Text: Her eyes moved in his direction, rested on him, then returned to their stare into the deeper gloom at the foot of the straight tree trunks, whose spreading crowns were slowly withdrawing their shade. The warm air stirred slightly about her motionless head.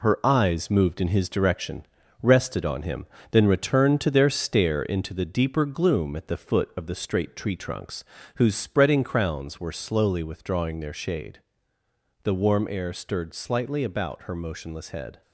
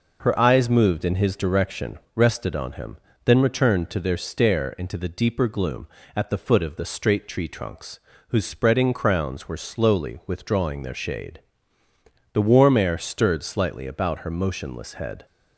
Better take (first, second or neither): second